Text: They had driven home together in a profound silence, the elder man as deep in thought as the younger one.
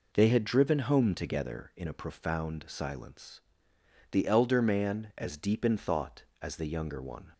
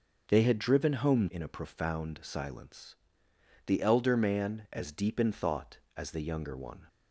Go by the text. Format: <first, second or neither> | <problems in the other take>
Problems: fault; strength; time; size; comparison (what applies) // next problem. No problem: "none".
first | skips "together"; at 1.2 s